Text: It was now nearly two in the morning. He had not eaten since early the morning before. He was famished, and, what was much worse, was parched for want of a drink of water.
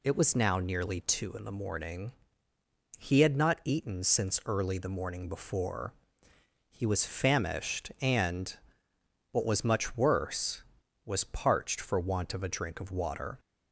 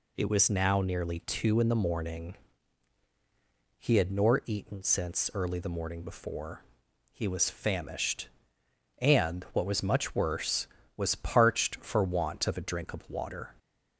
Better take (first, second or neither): first